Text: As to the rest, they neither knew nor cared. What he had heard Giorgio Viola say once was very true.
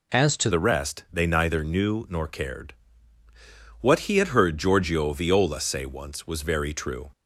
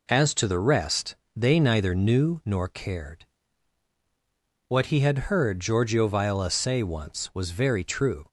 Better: second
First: changes voice at "the"; from 0.5 s on; 6.6 s long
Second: none

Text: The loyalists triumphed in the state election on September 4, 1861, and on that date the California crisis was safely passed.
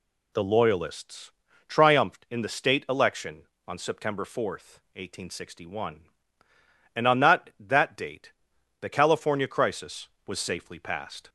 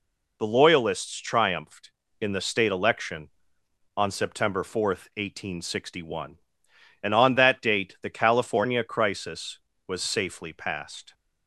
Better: second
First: pauses between "loyalists" and "triumphed"; slight; at 1.3 s; 0.36 s long // says "that" twice; at 7.5 s // pauses between "date" and "the"; noticeable; at 8.3 s; 0.48 s long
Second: none

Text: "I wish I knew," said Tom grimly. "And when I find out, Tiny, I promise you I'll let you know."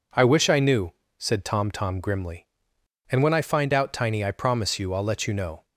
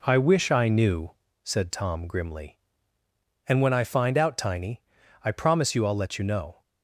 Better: second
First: says "Tom" twice; at 1.7 s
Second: none

